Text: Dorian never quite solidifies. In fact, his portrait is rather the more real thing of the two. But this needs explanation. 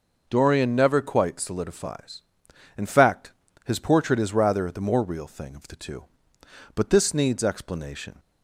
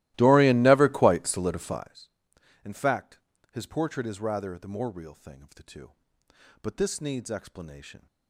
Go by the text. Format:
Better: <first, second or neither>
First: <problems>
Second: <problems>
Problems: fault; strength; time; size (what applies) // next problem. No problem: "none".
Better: first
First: none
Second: starts louder than the rest; strong; until 2.0 s; 16.5 dB